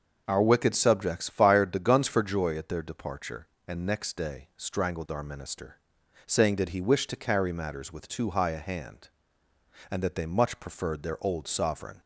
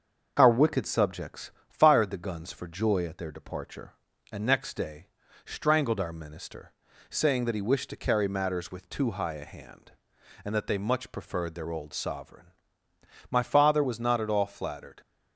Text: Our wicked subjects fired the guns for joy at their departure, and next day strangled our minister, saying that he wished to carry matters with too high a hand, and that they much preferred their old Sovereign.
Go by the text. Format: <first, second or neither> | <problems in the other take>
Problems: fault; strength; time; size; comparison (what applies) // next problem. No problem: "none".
first | starts louder than the rest; until 1.3 s; 6.5 dB; also in the first // pauses between "subjects" and "fired"; slight; at 1.4 s; 0.18 s long // pauses between "day" and "strangled"; slight; at 5.0 s; 0.36 s long // goes on to say "My father was not at all flattered"; strong; from 13.3 s on; 1.6 s long